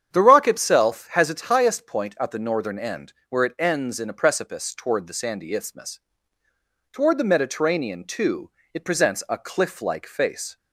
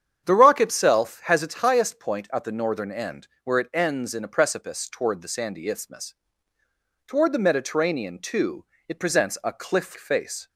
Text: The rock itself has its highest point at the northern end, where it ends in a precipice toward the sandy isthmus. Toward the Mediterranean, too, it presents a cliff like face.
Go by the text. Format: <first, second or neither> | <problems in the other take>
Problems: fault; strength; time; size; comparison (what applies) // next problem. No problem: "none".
first | starts louder than the rest; strong; until 1.2 s; 8.5 dB; strong in the first // skips "like"; at 9.9 s